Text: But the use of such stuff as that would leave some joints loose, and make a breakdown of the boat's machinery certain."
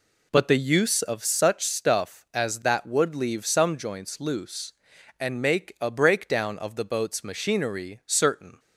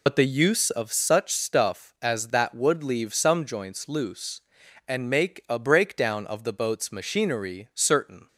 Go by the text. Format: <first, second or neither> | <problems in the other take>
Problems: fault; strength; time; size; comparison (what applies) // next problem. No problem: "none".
first | loses the start of "But"; at 0.0 s; 70 ms